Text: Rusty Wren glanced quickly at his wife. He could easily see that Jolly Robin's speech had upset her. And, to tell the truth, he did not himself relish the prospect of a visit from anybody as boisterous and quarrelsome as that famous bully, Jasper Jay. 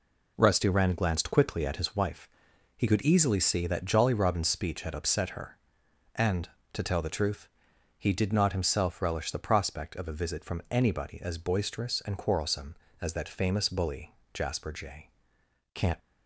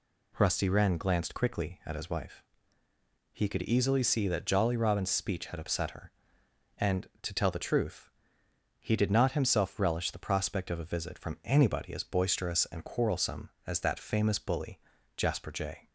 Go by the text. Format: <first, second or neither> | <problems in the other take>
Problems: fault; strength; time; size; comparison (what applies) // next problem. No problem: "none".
second | goes on to say "Can't"; slight; from 15.7 s on; 0.26 s long